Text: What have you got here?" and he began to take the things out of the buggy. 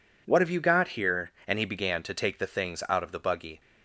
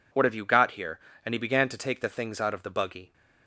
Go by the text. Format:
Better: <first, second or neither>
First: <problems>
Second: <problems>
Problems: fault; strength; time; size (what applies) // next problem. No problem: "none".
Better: neither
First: none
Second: none